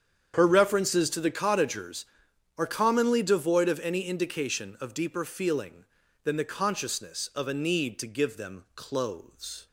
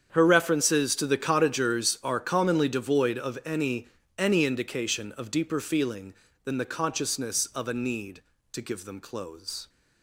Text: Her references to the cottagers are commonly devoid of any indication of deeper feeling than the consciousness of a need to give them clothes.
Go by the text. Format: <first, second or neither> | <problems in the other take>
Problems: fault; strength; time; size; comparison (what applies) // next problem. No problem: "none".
first | starts louder than the rest; strong; until 1.1 s; 8 dB; strong in the first // says "any" twice; at 4.1 s